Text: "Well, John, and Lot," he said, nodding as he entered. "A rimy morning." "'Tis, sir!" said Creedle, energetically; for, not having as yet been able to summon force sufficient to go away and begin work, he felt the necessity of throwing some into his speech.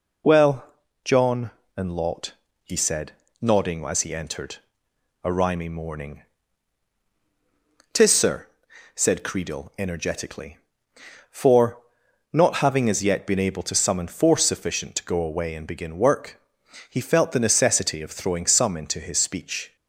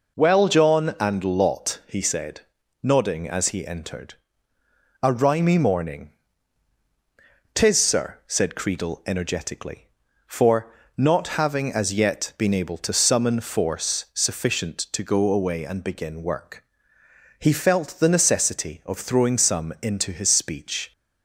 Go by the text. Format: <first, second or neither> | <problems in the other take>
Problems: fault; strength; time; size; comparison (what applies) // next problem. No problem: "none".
neither | none